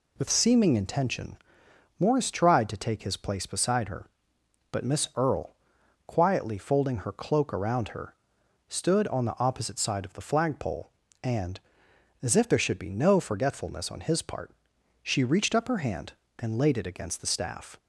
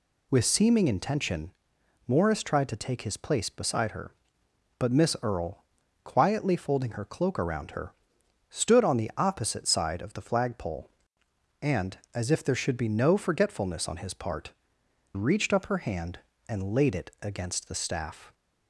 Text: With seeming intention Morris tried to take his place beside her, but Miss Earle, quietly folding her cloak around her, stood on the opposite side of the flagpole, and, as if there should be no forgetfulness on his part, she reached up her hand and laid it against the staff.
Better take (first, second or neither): first